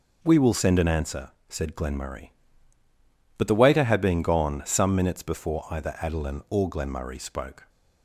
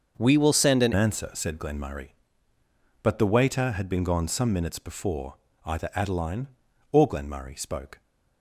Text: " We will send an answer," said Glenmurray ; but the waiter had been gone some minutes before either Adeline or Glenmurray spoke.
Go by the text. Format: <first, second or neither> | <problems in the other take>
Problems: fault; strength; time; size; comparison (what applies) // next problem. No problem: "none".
first | starts louder than the rest; until 1.1 s; 6.5 dB // changes voice from "We" to "an"; from 0.1 to 0.9 s; 0.8 s long // pauses between "before" and "either"; slight; at 5.3 s; 0.32 s long